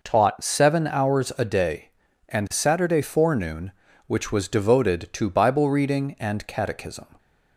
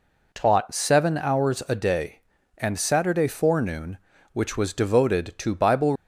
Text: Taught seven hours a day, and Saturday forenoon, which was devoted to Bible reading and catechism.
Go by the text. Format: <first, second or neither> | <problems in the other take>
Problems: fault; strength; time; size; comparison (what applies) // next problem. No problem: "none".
first | stops before "reading and catechism"; at 5.9 s